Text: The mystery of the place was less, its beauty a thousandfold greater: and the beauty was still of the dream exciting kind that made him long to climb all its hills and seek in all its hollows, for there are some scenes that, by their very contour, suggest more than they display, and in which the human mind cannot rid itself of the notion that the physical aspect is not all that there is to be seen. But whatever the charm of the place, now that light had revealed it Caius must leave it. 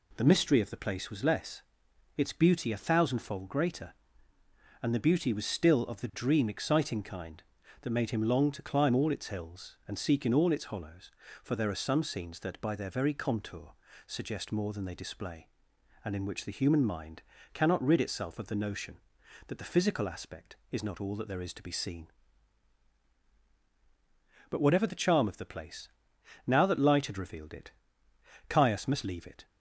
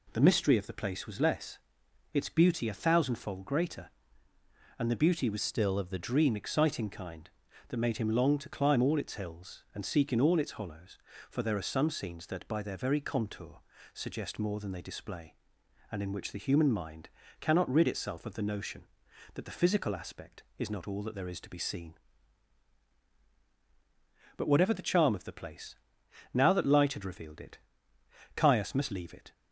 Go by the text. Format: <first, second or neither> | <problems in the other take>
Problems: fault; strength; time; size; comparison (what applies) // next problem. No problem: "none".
first | changes voice from "still" to "the"; from 5.4 to 5.9 s; 0.5 s long // pauses between "mind" and "cannot"; slight; at 17.0 s; 0.32 s long; slight in the first // pauses between "it" and "Caius"; noticeable; at 27.5 s; 0.76 s long; noticeable in the first